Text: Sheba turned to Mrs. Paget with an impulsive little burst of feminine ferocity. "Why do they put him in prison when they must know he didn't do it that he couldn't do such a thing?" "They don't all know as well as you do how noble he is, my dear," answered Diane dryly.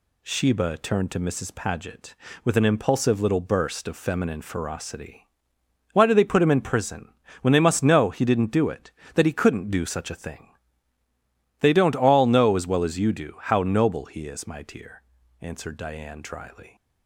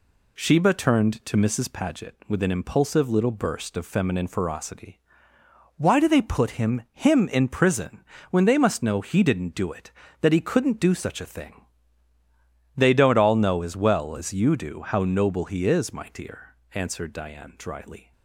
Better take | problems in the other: first | says "him" twice; at 6.9 s // pauses between "prison" and "when"; slight; at 8.0 s; 0.28 s long; slight in the first

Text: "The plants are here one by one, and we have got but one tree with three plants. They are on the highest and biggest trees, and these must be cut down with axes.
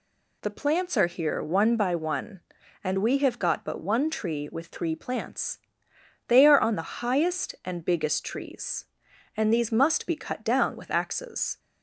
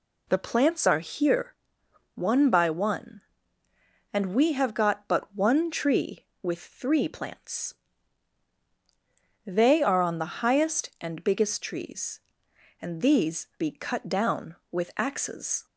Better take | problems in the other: first | pauses between "here" and "one"; noticeable; at 1.5 s; 0.62 s long // skips "must"; at 13.5 s

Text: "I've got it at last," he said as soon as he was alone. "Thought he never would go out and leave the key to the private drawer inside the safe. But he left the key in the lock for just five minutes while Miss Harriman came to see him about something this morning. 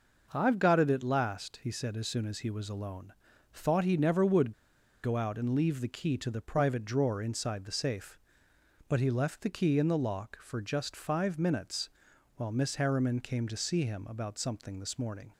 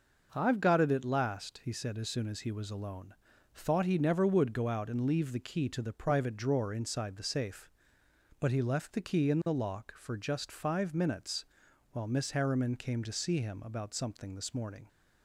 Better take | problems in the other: second | pauses between "would" and "go"; noticeable; at 4.5 s; 0.51 s long // pauses between "minutes" and "while"; noticeable; at 11.8 s; 0.46 s long; noticeable in the second

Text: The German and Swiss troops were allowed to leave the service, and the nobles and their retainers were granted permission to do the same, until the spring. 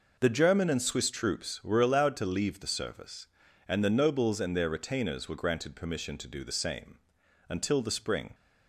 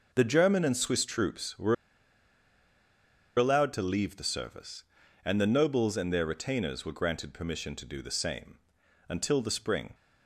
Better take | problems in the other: first | pauses between "were" and "allowed"; strong; at 1.7 s; 1.6 s long

